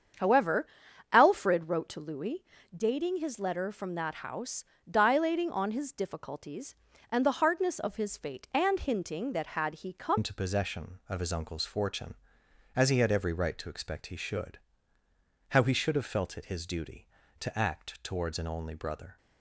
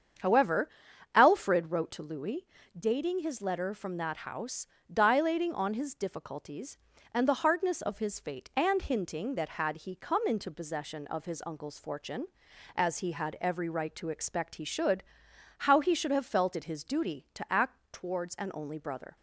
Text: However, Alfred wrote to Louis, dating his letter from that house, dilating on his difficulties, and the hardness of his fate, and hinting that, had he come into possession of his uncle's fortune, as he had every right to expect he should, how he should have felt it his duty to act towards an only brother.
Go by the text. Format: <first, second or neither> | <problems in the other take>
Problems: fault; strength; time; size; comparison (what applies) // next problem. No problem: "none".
second | starts louder than the rest; strong; until 1.6 s; 7.5 dB; strong in the second // changes voice at "into"; from 10.1 s on; 9.0 s long